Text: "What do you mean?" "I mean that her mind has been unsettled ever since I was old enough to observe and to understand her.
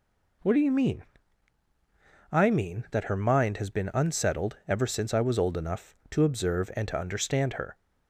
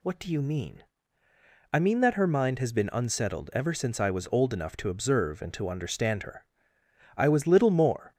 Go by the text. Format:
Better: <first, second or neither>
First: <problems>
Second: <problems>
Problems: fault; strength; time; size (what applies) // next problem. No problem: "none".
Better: first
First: none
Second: goes on to say "I was little more"; noticeable; from 7.1 s on; 0.98 s long